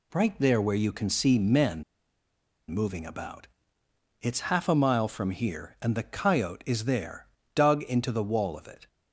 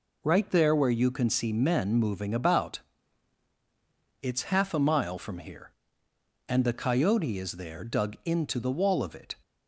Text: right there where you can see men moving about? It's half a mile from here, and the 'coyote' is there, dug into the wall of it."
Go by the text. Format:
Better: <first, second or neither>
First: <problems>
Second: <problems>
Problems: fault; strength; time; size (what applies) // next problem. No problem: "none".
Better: second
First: pauses between "men" and "moving"; noticeable; at 1.8 s; 0.87 s long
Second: none